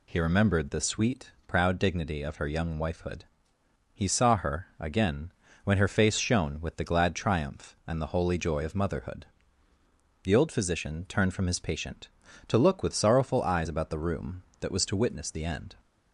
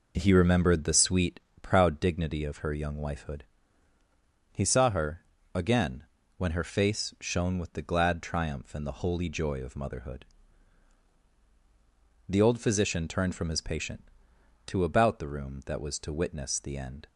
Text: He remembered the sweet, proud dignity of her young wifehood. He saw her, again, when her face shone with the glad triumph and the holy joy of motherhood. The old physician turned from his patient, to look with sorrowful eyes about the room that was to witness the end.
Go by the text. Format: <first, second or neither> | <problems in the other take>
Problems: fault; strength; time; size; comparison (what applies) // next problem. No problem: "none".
first | skips "look with sorrowful eyes"; at 14.8 s